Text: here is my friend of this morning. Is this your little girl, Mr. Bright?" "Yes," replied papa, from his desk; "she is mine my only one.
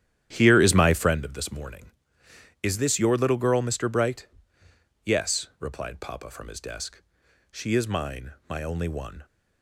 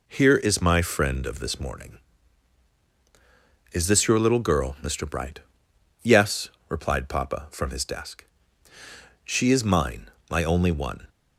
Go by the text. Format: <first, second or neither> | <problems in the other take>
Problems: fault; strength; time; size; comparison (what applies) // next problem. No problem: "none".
second | starts louder than the rest; strong; until 1.3 s; 11 dB // pauses between "mine" and "my"; slight; at 8.3 s; 0.16 s long; slight in the second